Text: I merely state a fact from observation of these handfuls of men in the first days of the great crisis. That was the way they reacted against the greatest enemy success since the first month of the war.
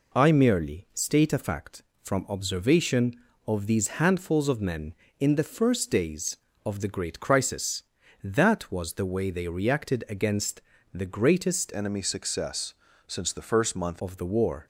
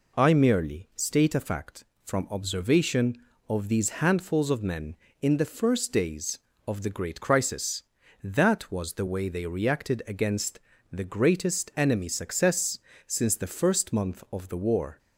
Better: second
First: pauses between "against" and "the"; slight; at 10.6 s; 0.30 s long // changes voice from "enemy" to "month"; from 11.7 to 14.0 s; 2.3 s long // pauses between "success" and "since"; slight; at 12.7 s; 0.32 s long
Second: pauses between "against" and "the"; slight; at 10.5 s; 0.30 s long // pauses between "success" and "since"; slight; at 12.7 s; 0.28 s long

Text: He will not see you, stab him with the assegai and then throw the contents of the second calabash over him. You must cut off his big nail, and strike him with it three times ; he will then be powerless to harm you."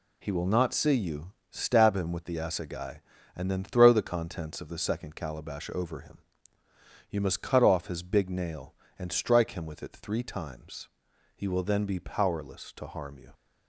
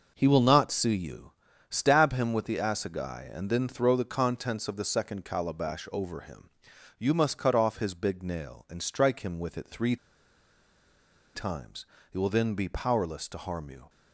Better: first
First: none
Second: pauses between "three" and "times"; strong; at 9.9 s; 1.3 s long

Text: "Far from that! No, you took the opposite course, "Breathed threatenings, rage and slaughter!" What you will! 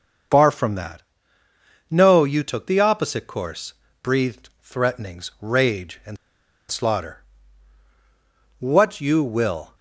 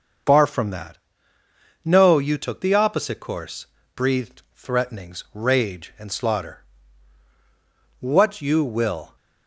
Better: second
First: starts louder than the rest; until 2.1 s; 6.5 dB // pauses between "and" and "slaughter"; noticeable; at 6.1 s; 0.54 s long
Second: starts louder than the rest; until 2.1 s; 6.5 dB

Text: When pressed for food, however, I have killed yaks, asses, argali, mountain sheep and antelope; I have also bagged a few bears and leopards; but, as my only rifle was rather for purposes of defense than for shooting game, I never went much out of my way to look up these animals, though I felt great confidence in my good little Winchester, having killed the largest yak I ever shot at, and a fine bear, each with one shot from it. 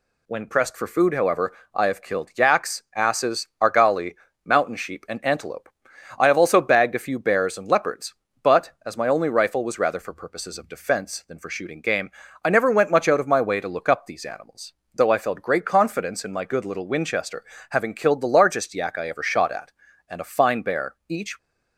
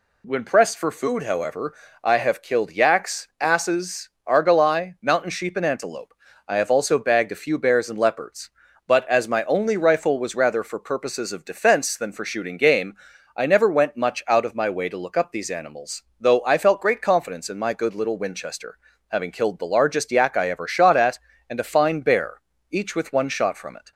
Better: second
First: stops before "with one shot from it"; at 21.3 s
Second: none

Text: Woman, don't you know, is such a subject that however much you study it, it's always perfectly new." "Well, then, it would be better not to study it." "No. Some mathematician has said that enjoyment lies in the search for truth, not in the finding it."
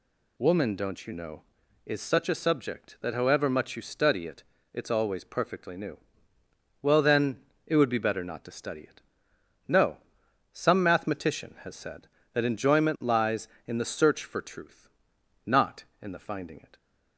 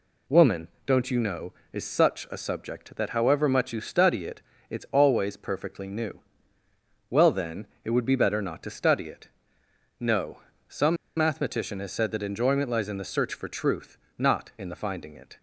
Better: first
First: none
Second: pauses between "Some" and "mathematician"; slight; at 10.9 s; 0.20 s long

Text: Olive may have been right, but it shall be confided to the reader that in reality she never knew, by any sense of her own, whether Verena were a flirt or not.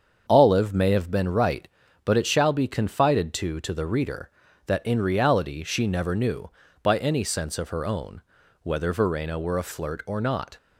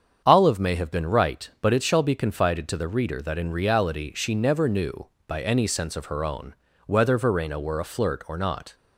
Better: second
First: starts louder than the rest; until 1.2 s; 7 dB // says "to" twice; at 3.6 s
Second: starts louder than the rest; strong; until 1.2 s; 7.5 dB

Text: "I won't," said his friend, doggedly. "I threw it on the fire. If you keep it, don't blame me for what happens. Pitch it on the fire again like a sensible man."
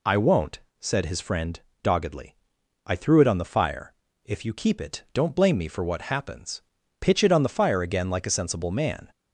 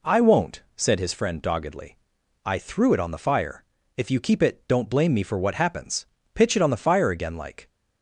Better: first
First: none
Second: stops before "a sensible man"; at 7.6 s

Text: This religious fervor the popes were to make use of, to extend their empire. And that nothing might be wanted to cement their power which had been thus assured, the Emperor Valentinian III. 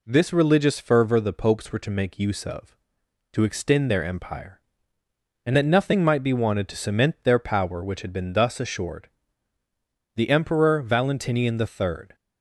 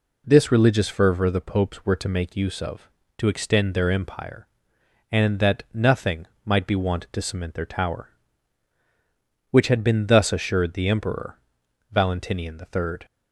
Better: first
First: none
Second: pauses between "nothing" and "might"; slight; at 6.2 s; 0.20 s long // says "tower" for "power"; at 7.6 s // pauses between "Emperor" and "Valentinian"; noticeable; at 11.3 s; 0.54 s long

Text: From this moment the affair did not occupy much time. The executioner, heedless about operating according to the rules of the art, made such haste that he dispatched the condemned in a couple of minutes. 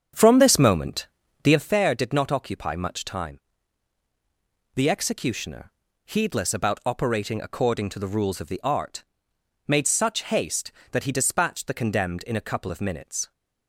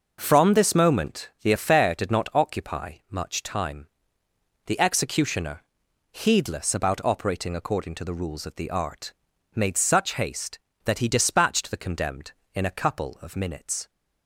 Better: second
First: starts louder than the rest; strong; until 1.7 s; 7.5 dB // pauses between "moment" and "the"; slight; at 1.0 s; 0.36 s long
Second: none

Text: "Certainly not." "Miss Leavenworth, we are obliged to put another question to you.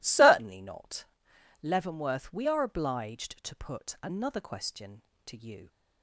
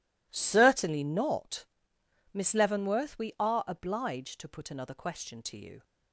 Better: second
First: skips "Miss"; at 1.3 s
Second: none

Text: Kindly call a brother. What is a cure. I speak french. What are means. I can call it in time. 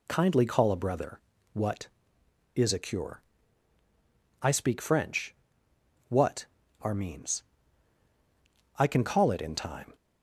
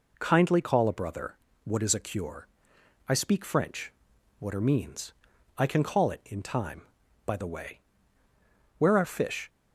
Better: first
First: none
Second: goes on to say "By the way where are fish"; strong; from 7.2 s on; 2.2 s long

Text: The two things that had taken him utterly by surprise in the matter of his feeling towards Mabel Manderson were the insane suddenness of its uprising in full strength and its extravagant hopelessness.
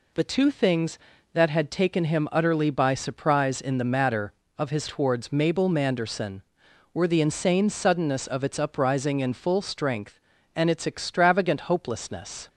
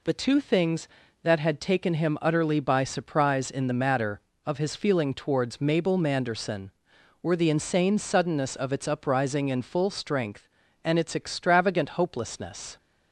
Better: second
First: skips "feeling"; at 4.8 s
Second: none

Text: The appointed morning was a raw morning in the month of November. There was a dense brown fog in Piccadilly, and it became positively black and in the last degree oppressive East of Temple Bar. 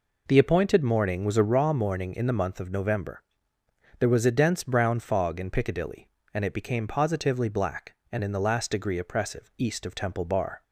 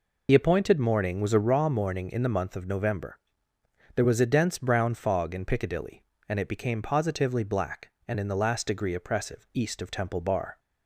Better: first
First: none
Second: loses the start of "The"; at 0.2 s; 50 ms

